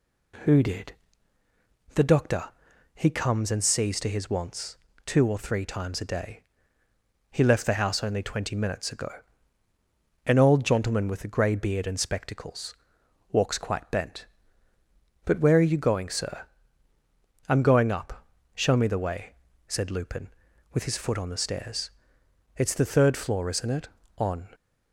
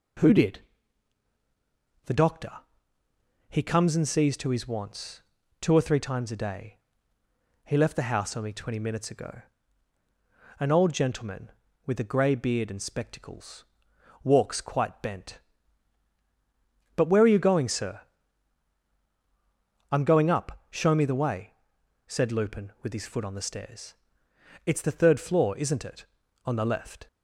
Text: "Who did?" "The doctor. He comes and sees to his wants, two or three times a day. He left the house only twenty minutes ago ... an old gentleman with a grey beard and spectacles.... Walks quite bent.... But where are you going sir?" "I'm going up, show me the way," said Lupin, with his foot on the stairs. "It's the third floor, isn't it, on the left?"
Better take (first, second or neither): second